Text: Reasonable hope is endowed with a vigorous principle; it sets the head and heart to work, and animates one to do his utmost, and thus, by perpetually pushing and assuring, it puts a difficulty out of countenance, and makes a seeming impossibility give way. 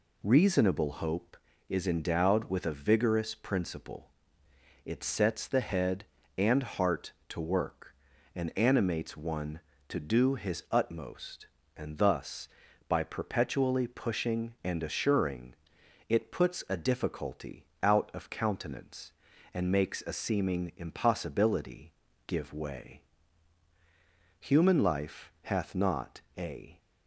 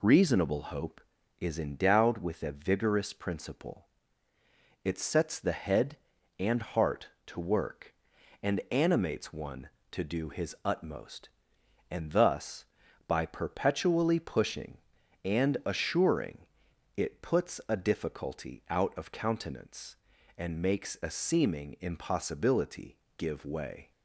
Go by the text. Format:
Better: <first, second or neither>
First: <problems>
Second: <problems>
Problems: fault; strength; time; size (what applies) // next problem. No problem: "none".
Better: second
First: pauses between "difficulty" and "out"; slight; at 17.6 s; 0.16 s long // pauses between "impossibility" and "give"; slight; at 21.9 s; 0.34 s long // goes on to say "Human life hath not a"; strong; from 24.3 s on; 2.4 s long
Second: pauses between "impossibility" and "give"; slight; at 22.9 s; 0.22 s long